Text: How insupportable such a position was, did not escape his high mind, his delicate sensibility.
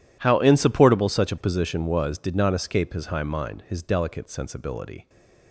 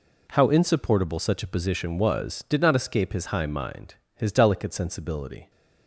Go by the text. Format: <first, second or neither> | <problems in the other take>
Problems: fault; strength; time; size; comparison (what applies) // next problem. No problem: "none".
neither | none